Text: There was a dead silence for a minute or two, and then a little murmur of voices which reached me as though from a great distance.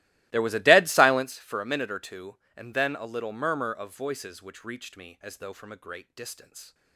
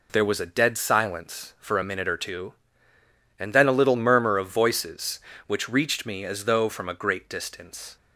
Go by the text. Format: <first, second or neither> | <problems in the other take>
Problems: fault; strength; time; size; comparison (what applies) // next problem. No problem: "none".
second | starts louder than the rest; strong; until 1.4 s; 19 dB